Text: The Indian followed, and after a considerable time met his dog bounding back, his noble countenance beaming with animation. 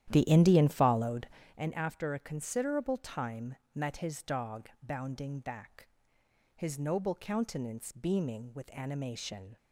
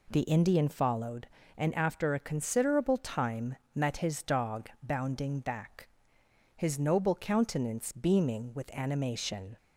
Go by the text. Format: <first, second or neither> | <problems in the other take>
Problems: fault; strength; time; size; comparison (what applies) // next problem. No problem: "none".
second | starts louder than the rest; strong; until 1.6 s; 11.5 dB // pauses between "time" and "met"; slight; at 3.5 s; 0.18 s long; slight in the second